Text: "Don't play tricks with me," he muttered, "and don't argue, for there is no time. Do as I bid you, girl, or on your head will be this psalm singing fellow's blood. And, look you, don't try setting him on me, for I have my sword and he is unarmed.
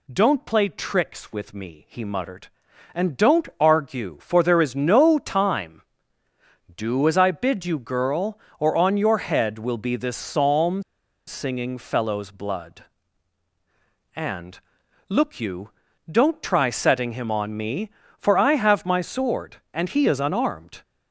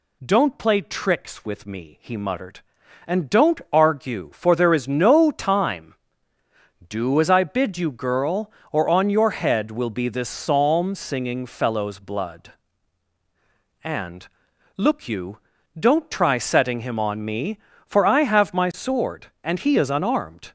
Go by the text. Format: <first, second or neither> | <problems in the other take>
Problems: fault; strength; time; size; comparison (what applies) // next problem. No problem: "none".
second | pauses between "psalm" and "singing"; at 10.8 s; 0.45 s long